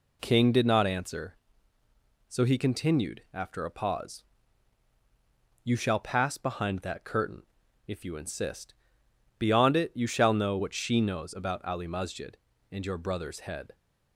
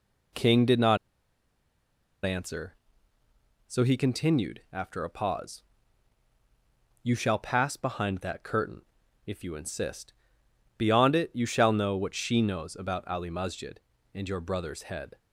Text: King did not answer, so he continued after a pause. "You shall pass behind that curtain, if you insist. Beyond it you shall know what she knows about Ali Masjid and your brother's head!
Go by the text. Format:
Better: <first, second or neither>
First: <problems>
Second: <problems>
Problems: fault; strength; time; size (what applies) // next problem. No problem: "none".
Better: first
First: none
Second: pauses between "not" and "answer"; strong; at 0.9 s; 1.2 s long